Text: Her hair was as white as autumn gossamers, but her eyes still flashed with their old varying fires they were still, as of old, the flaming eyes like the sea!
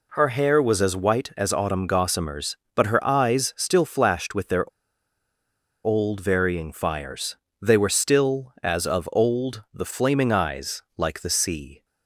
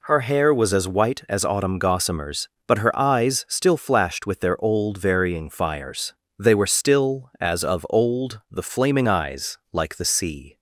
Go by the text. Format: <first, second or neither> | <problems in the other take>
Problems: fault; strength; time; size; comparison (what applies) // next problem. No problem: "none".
second | pauses between "their" and "old"; at 4.6 s; 1.1 s long // pauses between "fires" and "they"; slight; at 7.3 s; 0.26 s long; slight in the second